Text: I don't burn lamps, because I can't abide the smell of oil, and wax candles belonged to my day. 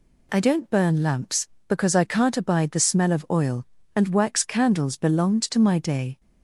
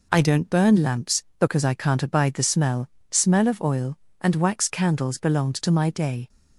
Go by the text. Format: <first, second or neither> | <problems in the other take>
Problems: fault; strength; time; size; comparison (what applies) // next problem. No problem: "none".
first | says "smell" twice; at 3.1 s